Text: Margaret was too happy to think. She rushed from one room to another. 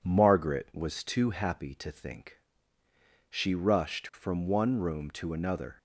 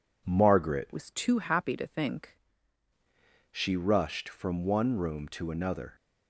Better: first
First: none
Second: changes voice from "was" to "think"; from 0.9 to 2.3 s; 1.4 s long

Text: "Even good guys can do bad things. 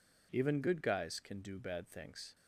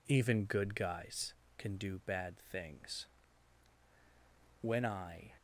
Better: first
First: none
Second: goes on to say "When I"; noticeable; from 4.6 s on; 0.76 s long

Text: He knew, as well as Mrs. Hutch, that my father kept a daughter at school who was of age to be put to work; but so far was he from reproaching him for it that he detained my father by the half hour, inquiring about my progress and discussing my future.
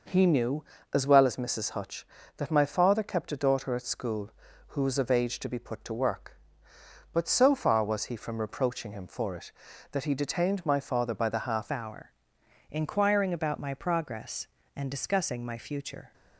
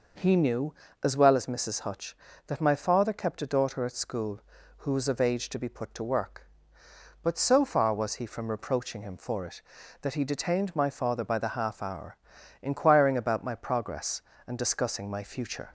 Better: second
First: changes voice at "hour"; from 11.7 s on; 4.4 s long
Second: none

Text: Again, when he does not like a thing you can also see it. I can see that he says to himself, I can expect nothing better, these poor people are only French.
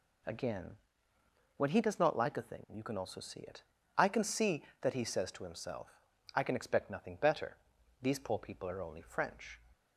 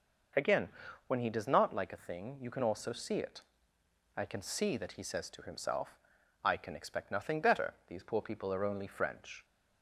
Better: neither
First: none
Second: none

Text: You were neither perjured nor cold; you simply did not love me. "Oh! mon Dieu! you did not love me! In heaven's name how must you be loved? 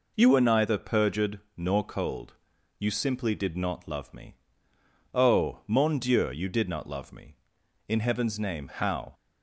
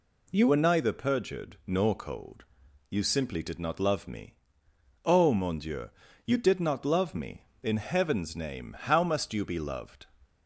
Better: second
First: pauses between "perjured" and "nor"; slight; at 1.3 s; 0.16 s long // stops before "must you be loved"; at 9.1 s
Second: none

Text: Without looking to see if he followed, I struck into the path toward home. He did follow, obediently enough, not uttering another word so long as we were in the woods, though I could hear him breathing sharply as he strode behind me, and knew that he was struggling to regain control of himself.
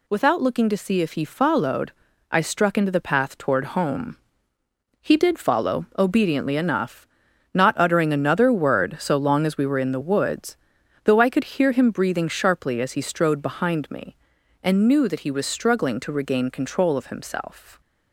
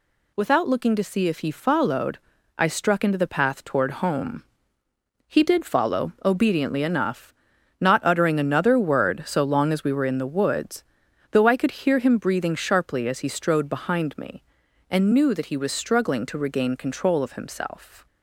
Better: neither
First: none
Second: none

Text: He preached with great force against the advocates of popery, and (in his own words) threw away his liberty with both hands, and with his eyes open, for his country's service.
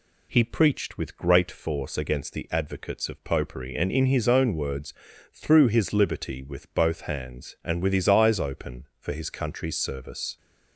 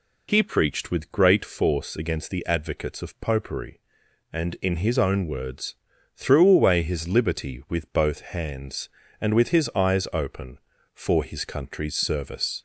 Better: second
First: skips "away"; at 5.6 s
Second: none

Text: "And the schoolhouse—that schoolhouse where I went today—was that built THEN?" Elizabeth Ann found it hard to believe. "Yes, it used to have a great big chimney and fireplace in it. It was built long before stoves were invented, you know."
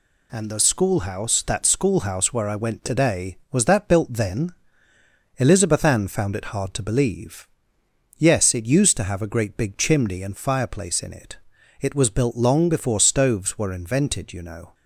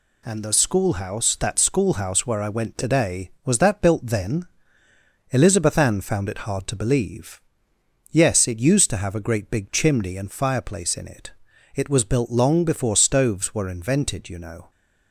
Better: neither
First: none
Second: none

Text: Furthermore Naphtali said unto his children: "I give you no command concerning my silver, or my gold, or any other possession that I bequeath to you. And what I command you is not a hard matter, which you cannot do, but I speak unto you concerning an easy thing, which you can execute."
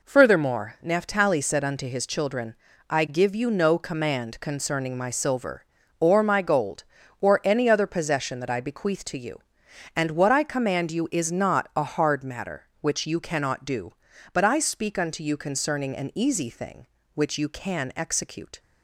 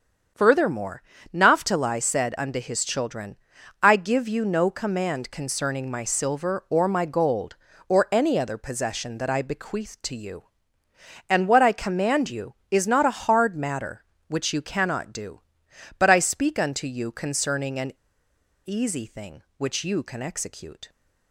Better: first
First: none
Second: starts louder than the rest; strong; until 1.6 s; 7.5 dB // pauses between "Furthermore" and "Naphtali"; slight; at 1.0 s; 0.32 s long // pauses between "an" and "easy"; noticeable; at 17.9 s; 0.73 s long

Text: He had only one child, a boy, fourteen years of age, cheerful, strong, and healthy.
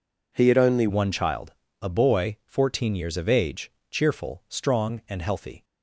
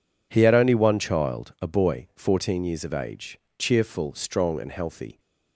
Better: second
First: changes voice at "one"; from 0.8 s on; 4.8 s long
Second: none

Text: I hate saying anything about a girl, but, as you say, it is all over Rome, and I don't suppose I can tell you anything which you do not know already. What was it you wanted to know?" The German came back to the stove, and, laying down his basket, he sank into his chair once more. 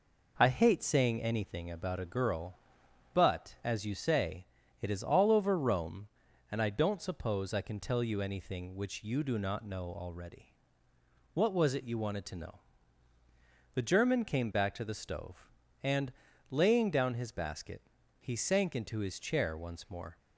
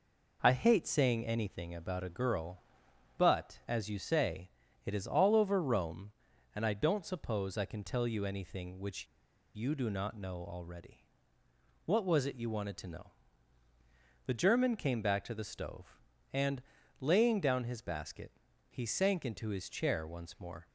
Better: first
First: none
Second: pauses between "which" and "you"; noticeable; at 9.0 s; 0.47 s long

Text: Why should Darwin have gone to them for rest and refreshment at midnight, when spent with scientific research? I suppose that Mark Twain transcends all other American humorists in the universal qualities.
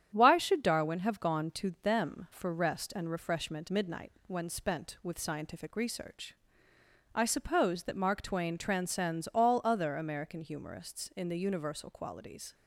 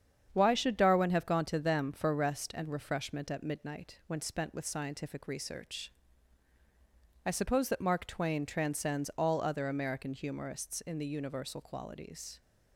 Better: second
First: starts louder than the rest; strong; until 1.1 s; 9 dB // skips "at"; at 3.6 s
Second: starts louder than the rest; strong; until 1.3 s; 8 dB

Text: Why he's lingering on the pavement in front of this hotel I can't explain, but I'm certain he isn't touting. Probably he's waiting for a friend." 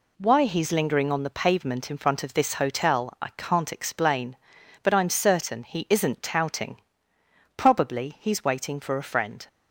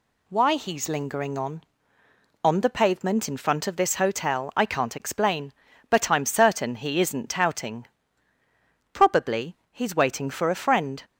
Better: first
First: none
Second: says "on" twice; at 2.4 s // pauses between "Probably" and "he's"; slight; at 9.5 s; 0.16 s long

